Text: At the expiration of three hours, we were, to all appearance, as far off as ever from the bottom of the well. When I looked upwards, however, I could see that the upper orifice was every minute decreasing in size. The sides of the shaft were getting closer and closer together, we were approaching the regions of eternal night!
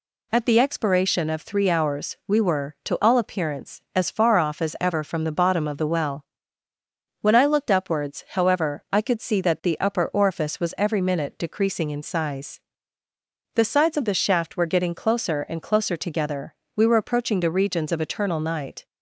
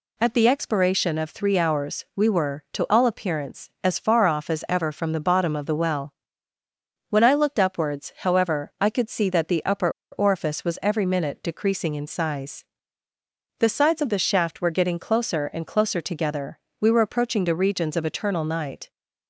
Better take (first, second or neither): first